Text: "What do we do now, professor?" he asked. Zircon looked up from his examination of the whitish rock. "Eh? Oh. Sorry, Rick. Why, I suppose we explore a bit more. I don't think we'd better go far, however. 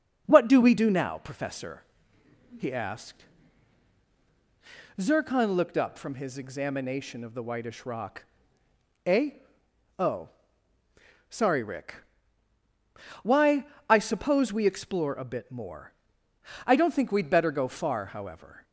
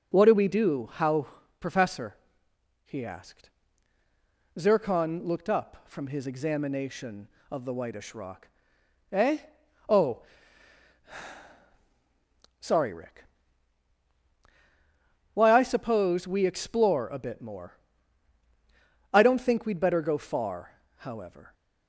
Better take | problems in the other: first | says "how" for "now"; at 0.9 s

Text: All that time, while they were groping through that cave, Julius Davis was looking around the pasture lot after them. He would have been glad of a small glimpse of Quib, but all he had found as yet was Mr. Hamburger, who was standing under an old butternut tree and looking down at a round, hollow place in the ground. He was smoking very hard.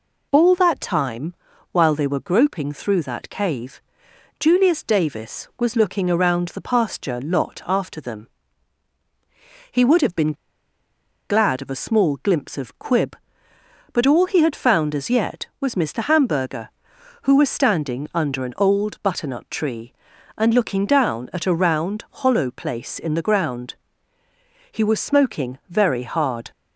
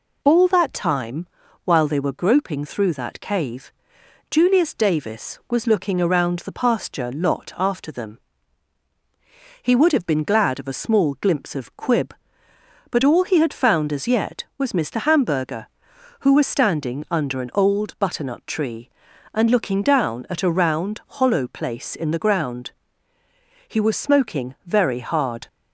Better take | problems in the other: second | pauses between "been" and "glad"; noticeable; at 10.3 s; 0.96 s long

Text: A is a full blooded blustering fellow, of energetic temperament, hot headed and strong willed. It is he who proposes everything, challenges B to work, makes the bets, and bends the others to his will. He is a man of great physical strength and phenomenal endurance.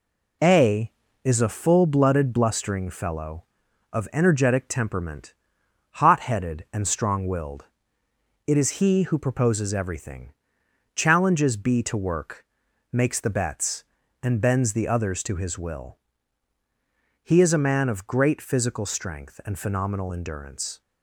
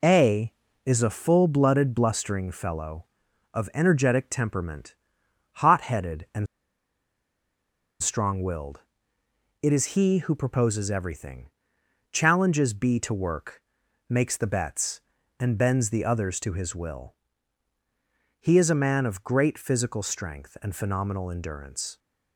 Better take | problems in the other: first | pauses between "and" and "strong"; strong; at 6.4 s; 1.5 s long

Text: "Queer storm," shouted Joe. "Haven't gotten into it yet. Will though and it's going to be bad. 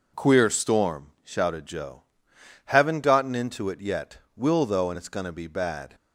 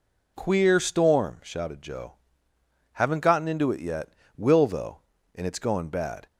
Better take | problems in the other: first | skips "to be"; at 5.9 s

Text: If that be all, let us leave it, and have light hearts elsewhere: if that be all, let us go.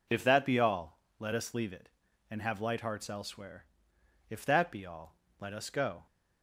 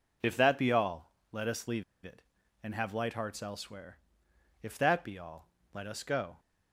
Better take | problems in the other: first | pauses between "leave" and "it"; slight; at 1.8 s; 0.21 s long

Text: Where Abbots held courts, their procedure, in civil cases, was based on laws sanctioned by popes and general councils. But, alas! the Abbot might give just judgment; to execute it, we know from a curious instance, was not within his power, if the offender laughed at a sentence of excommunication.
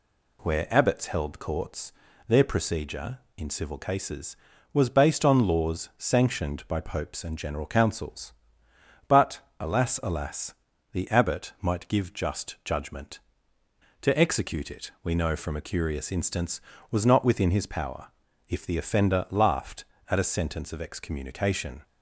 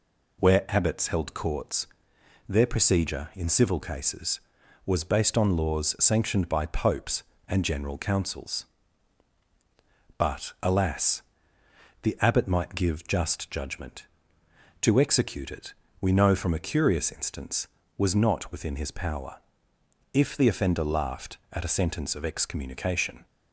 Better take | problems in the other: second | says "alas" twice; at 10.0 s

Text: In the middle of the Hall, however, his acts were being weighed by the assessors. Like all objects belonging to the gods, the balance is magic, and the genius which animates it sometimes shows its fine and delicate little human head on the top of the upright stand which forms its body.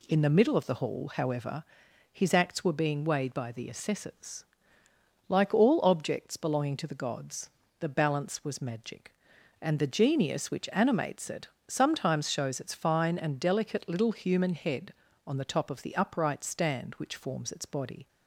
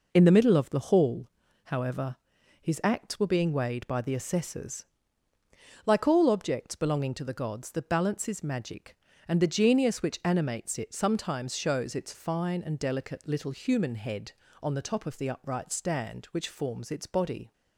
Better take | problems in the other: second | says "was" for "is"; at 8.4 s // pauses between "it" and "sometimes"; slight; at 11.4 s; 0.20 s long

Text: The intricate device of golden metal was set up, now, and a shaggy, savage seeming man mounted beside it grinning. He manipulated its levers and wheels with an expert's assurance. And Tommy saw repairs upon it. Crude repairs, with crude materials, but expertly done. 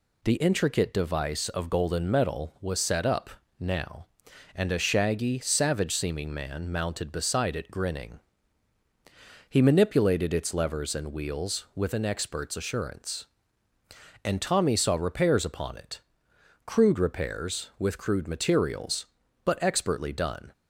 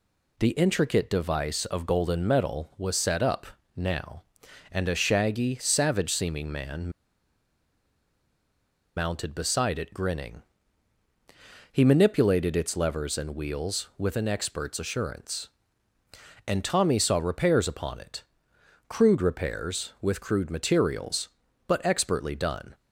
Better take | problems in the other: first | pauses between "man" and "mounted"; strong; at 6.9 s; 2.0 s long

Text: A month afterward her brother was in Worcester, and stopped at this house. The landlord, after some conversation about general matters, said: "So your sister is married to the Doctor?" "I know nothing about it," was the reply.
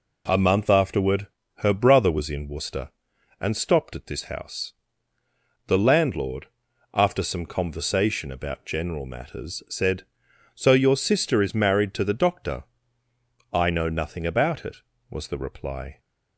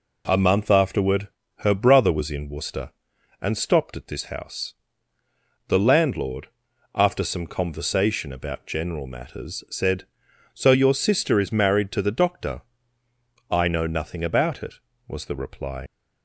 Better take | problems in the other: first | pauses between "afterward" and "her"; slight; at 1.2 s; 0.30 s long; slight in the first // leaves "reply" unfinished; at 15.8 s; 105 ms

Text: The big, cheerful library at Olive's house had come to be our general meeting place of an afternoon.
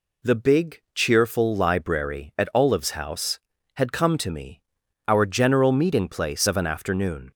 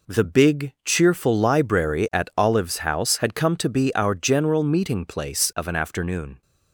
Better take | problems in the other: second | says "me" for "be"; at 4.3 s

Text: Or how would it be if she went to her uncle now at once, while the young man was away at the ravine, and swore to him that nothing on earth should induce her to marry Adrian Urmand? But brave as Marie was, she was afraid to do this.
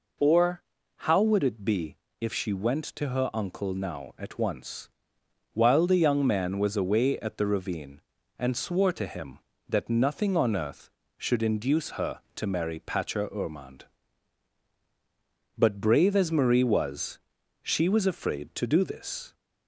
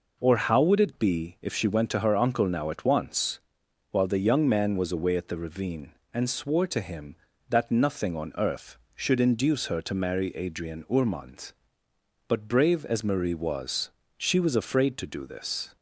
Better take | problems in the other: second | pauses between "Or" and "how"; slight; at 0.6 s; 0.36 s long // pauses between "be" and "if"; slight; at 1.9 s; 0.24 s long // says "Patcher" for "Adrian"; at 12.7 s

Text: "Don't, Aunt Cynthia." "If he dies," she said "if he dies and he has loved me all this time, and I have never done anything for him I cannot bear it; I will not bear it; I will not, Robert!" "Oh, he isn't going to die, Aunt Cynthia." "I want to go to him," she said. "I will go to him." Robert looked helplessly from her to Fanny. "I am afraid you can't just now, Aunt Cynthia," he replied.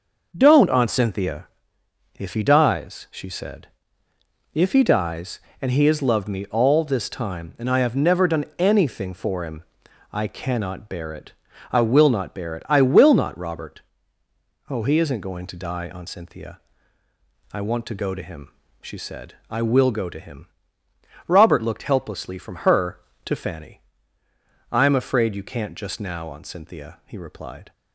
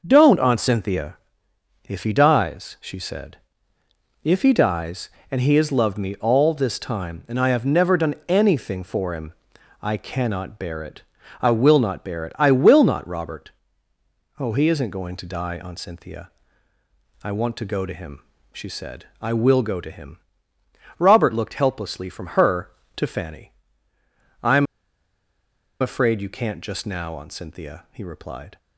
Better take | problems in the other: first | starts louder than the rest; noticeable; until 1.0 s; 6 dB; noticeable in the first // pauses between "said" and "if"; noticeable; at 3.3 s; 0.86 s long; noticeable in the first // pauses between "him" and "I"; noticeable; at 9.3 s; 0.48 s long; noticeable in the first // pauses between "am" and "afraid"; at 24.6 s; 1.1 s long

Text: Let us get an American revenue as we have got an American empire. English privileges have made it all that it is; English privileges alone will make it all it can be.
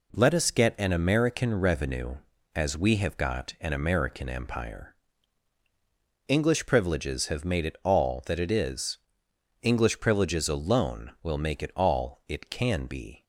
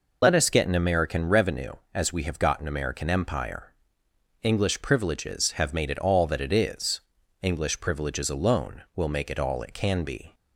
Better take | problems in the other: first | loses the start of "Let"; at 0.2 s; 35 ms

